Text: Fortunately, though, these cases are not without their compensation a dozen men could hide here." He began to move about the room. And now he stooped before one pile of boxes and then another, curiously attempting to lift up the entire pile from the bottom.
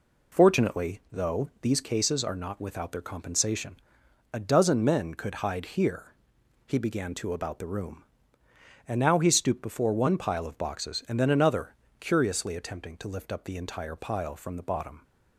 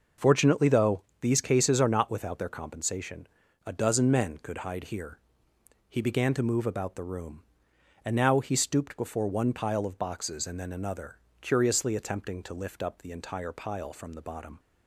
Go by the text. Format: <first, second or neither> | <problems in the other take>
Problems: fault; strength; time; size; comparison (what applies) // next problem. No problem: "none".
second | pauses between "compensation" and "a"; noticeable; at 3.7 s; 0.58 s long; also in the second // skips "move"; at 7.3 s